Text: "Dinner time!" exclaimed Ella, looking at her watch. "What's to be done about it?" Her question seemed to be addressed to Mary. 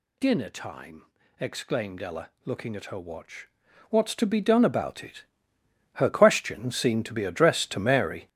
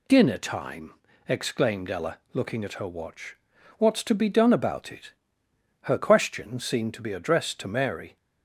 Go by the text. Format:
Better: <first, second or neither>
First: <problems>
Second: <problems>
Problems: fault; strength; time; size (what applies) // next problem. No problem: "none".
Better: second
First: gets louder; strong; throughout; 9 dB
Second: none